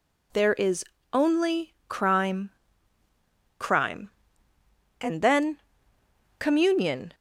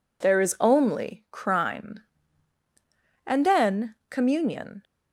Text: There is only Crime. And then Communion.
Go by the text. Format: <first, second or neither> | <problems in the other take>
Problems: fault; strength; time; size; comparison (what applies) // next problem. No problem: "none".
second | pauses between "is" and "only"; slight; at 0.8 s; 0.28 s long // says "Crime" twice; at 3.5 s // pauses between "then" and "Communion"; noticeable; at 5.6 s; 0.78 s long